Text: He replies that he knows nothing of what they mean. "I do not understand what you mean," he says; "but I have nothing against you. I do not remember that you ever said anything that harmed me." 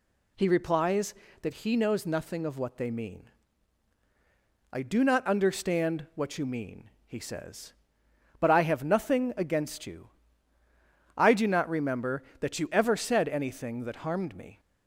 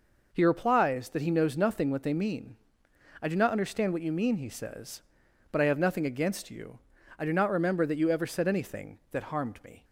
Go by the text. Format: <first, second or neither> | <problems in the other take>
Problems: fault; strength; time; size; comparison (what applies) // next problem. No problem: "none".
first | skips "of"; at 1.8 s